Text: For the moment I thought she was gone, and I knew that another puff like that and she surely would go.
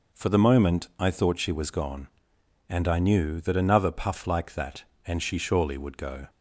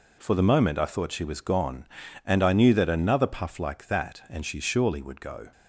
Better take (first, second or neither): neither